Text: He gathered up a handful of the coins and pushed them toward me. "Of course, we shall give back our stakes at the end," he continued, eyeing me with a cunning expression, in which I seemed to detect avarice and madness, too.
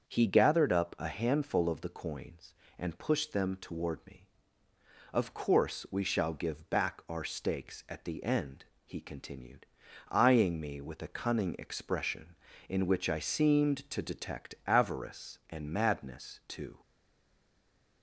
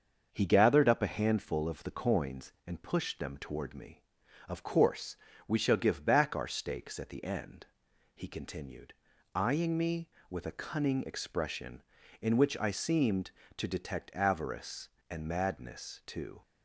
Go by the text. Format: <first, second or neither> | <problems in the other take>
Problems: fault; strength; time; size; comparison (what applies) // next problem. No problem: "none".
second | starts louder than the rest; until 1.1 s; 7 dB; also in the second // stays silent after the last word; noticeable; from 16.8 s on; 1.2 s long